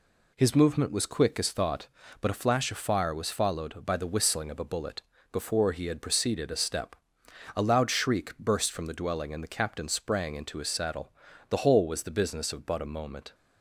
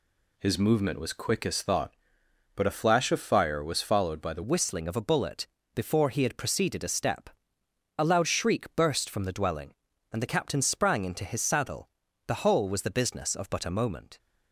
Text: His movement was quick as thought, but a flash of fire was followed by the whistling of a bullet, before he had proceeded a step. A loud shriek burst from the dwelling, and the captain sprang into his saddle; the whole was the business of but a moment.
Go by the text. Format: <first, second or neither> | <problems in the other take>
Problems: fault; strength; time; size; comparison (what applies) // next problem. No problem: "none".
first | changes voice at "whistling"; from 4.4 s on; 9.7 s long